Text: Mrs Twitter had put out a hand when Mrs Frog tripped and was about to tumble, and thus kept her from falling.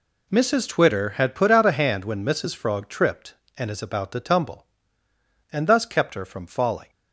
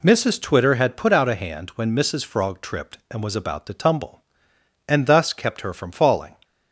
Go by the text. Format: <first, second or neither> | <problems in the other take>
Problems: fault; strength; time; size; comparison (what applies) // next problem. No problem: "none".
second | says "is" for "was"; at 3.6 s